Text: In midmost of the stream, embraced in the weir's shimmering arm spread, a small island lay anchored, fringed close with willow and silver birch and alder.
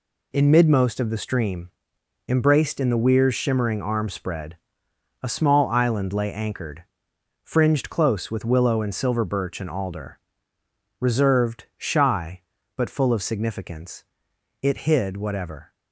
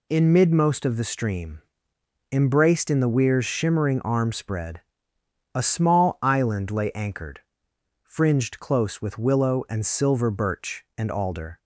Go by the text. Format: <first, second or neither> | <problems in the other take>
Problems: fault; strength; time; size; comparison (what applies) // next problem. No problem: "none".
second | goes on to say "Reserved shy but full of significance it hid whatever"; strong; from 11.0 s on; 4.7 s long